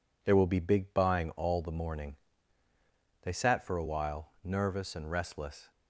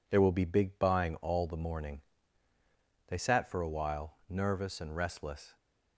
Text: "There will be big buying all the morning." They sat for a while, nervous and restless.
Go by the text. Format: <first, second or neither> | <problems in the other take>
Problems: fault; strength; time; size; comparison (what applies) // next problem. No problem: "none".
neither | none